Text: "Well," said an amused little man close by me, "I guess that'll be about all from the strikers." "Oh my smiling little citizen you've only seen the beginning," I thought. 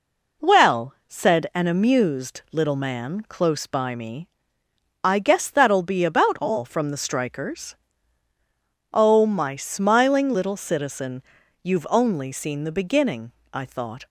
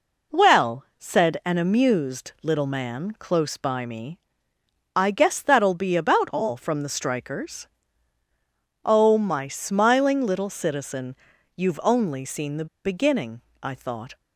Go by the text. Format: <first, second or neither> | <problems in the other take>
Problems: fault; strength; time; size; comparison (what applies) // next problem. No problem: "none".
first | pauses between "citizen" and "you've"; at 11.1 s; 0.42 s long; also in the first // pauses between "the" and "beginning"; slight; at 12.6 s; 0.19 s long